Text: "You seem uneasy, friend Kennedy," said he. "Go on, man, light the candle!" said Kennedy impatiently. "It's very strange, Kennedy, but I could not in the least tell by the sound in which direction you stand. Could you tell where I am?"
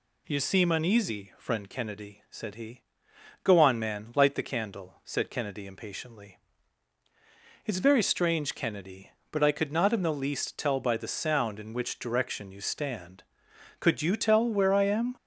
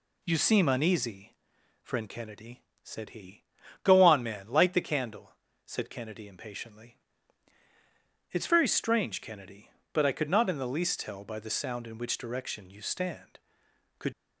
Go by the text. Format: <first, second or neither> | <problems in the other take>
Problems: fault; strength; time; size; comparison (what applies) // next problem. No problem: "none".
first | stops before "you tell where I am"; at 14.1 s